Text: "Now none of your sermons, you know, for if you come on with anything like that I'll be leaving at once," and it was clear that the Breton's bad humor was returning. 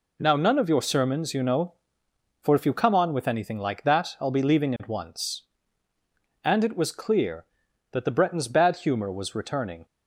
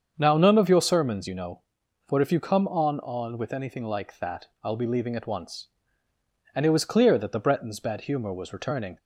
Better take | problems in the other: first | starts louder than the rest; strong; until 1.1 s; 7 dB // says "on" twice; at 3.0 s // pauses between "that" and "I'll"; slight; at 4.4 s; 0.16 s long

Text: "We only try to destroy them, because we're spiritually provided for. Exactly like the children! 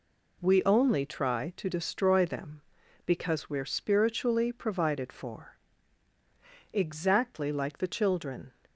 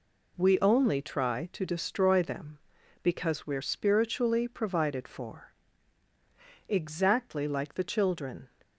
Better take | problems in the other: neither | none

